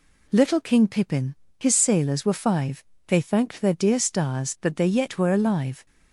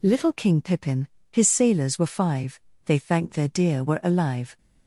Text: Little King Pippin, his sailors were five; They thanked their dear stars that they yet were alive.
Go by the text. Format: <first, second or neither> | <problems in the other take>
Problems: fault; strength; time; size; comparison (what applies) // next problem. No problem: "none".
first | skips "stars that they yet"; at 3.8 s